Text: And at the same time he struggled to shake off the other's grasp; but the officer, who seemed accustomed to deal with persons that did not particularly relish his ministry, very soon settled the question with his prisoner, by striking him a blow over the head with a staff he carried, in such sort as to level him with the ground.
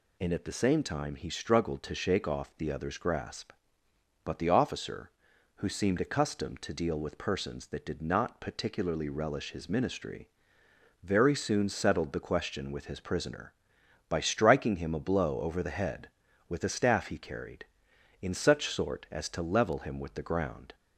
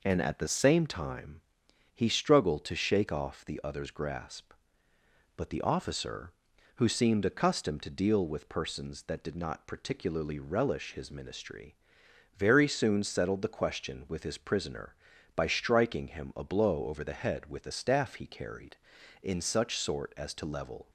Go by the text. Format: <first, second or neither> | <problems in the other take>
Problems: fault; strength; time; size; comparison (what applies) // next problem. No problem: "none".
first | pauses between "time" and "he"; noticeable; at 1.4 s; 0.52 s long // stops before "him with the ground"; at 20.8 s